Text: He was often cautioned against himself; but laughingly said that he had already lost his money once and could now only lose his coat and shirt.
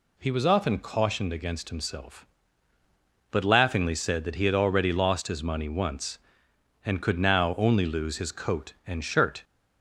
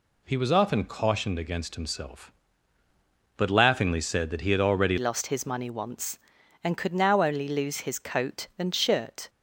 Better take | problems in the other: first | changes voice at "lost"; from 4.9 s on; 4.3 s long

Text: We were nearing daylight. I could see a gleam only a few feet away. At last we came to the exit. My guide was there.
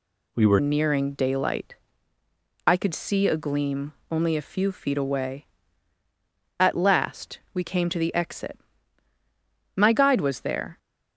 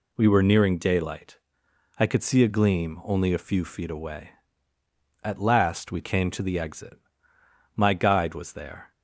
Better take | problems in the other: second | changes voice at "nearing"; from 0.5 s on; 10.2 s long // pauses between "gleam" and "only"; slight; at 3.9 s; 0.16 s long

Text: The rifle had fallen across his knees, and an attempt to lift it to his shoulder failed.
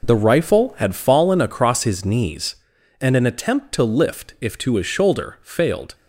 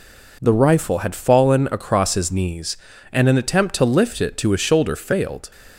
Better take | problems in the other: second | says "if" for "it"; at 4.3 s

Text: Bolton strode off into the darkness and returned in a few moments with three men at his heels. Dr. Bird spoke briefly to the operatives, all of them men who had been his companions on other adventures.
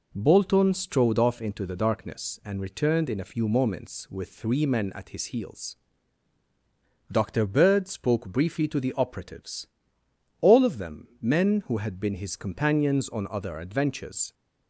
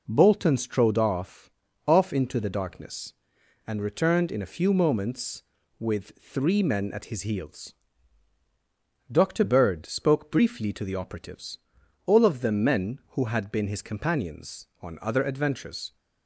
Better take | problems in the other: first | says "off" twice; at 1.8 s

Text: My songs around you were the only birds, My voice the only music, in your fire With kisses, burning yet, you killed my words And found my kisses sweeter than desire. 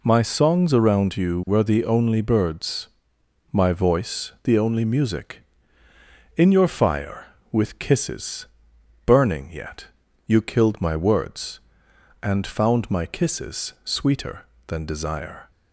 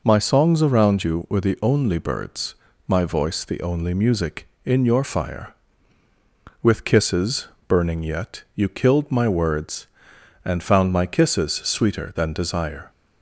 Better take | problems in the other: neither | none

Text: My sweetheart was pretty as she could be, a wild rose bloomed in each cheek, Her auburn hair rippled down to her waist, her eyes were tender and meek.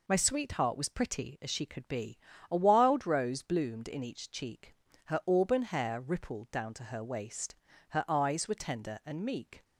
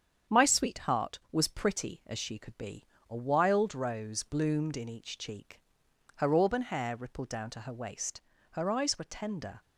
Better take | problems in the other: first | starts louder than the rest; strong; until 1.4 s; 8 dB // stops before "and meek"; at 9.6 s

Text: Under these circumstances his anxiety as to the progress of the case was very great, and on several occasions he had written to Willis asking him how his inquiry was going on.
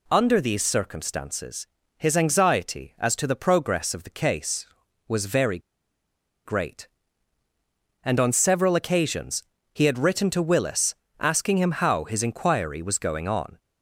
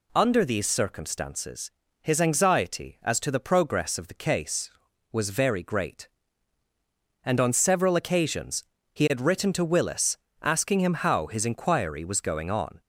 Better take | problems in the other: second | pauses between "circumstances" and "his"; slight; at 1.6 s; 0.32 s long; slight in the second // pauses between "very" and "great"; noticeable; at 5.5 s; 0.88 s long // pauses between "occasions" and "he"; slight; at 9.4 s; 0.28 s long; slight in the second // pauses between "Willis" and "asking"; slight; at 10.9 s; 0.26 s long; slight in the second

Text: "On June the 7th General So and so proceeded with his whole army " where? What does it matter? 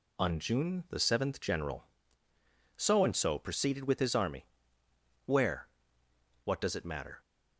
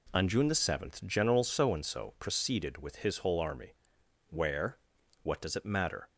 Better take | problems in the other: second | skips "whole"; at 4.1 s

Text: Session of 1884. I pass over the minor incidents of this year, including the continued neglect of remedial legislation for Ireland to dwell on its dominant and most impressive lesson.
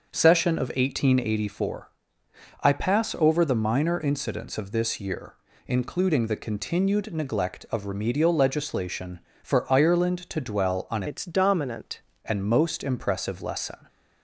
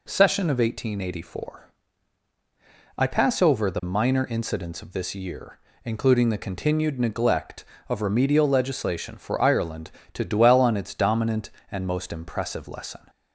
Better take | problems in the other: second | starts louder than the rest; noticeable; until 1.1 s; 6 dB // changes voice from "its" to "dominant"; from 11.0 to 11.9 s; 0.9 s long

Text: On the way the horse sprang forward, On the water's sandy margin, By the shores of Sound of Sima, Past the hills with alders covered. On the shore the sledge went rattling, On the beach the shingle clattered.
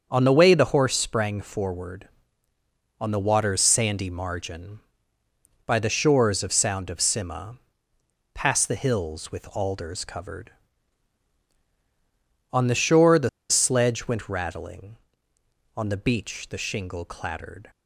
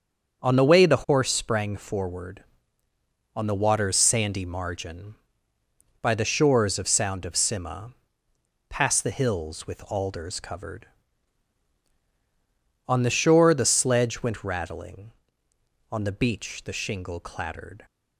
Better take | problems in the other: second | starts louder than the rest; until 1.1 s; 7 dB; also in the second // pauses between "the" and "sledge"; slight; at 13.2 s; 0.20 s long

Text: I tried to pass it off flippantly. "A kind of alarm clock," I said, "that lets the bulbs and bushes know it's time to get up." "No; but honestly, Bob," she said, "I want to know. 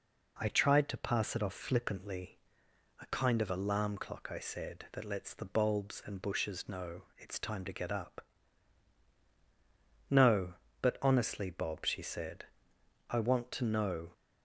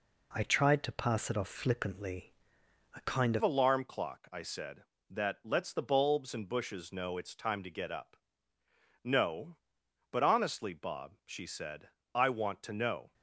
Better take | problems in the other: first | changes voice at "alarm"; from 3.4 s on; 9.7 s long

